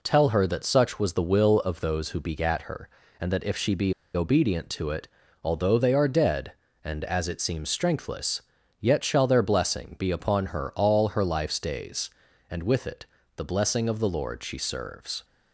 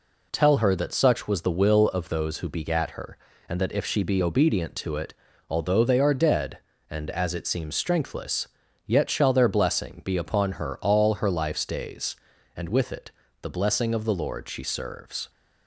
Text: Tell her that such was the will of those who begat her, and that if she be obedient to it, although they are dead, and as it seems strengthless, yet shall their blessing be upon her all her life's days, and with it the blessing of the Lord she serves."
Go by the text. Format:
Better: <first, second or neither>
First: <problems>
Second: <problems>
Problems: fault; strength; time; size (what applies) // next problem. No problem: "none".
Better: second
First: pauses between "be" and "obedient"; slight; at 3.9 s; 0.21 s long // pauses between "it" and "the"; slight; at 13.0 s; 0.30 s long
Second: pauses between "it" and "the"; slight; at 13.1 s; 0.30 s long